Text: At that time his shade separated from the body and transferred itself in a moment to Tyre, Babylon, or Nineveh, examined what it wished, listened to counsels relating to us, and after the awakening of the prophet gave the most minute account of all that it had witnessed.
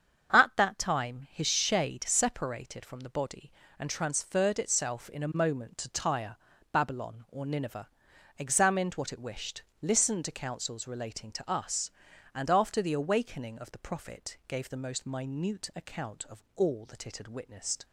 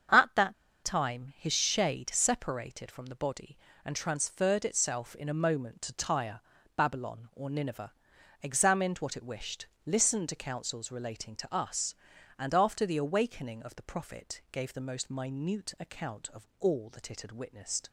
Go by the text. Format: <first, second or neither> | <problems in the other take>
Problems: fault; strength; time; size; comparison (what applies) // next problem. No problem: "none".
first | starts louder than the rest; strong; until 1.4 s; 7.5 dB; strong in the first // pauses between "that" and "time"; slight; at 0.5 s; 0.30 s long